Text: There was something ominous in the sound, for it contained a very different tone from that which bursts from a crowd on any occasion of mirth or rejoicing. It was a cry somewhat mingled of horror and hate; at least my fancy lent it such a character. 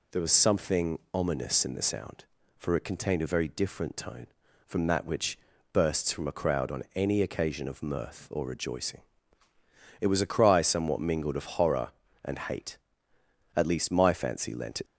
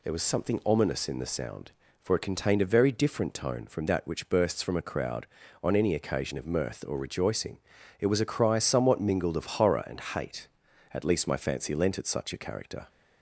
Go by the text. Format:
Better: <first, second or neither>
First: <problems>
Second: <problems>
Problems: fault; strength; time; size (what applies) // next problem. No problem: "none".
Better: second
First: pauses between "something" and "ominous"; slight; at 0.9 s; 0.16 s long // pauses between "which" and "bursts"; slight; at 5.3 s; 0.34 s long // stops before "such a character"; at 14.8 s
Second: none